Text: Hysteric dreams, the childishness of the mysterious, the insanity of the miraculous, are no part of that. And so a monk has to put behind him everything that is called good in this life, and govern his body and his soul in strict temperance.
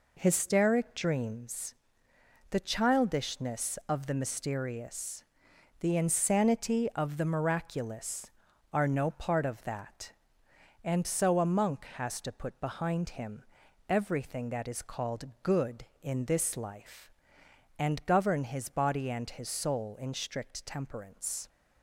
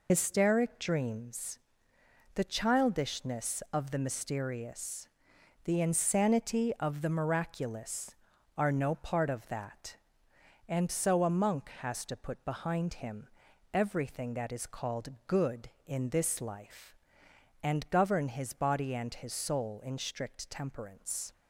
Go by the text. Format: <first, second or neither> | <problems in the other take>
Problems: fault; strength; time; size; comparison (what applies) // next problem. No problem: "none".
first | loses the start of "Hysteric"; at 0.0 s; 90 ms // pauses between "him" and "everything"; at 13.2 s; 0.44 s long; also in the first // pauses between "called" and "good"; slight; at 15.0 s; 0.18 s long; slight in the first